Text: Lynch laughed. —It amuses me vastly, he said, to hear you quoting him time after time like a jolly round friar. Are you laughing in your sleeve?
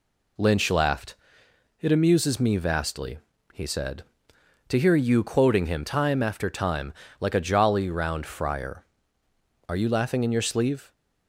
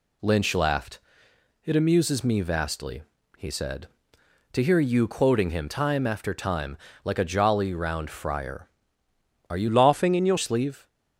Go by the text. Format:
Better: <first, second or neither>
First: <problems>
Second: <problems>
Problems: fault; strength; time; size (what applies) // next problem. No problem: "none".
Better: first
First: pauses between "time" and "like"; slight; at 6.9 s; 0.28 s long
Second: pauses between "time" and "like"; slight; at 6.7 s; 0.28 s long // changes voice from "laughing" to "your"; from 9.6 to 10.3 s; 0.7 s long